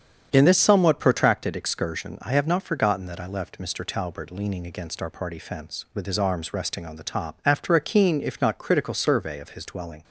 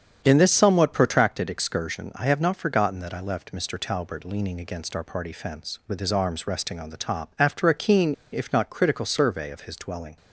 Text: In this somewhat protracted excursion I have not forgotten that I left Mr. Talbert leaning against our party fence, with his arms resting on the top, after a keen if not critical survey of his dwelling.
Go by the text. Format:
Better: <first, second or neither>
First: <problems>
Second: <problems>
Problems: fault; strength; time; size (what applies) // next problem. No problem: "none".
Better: first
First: starts louder than the rest; strong; until 1.3 s; 8 dB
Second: starts louder than the rest; strong; until 1.2 s; 8 dB // pauses between "keen" and "if"; slight; at 8.1 s; 0.18 s long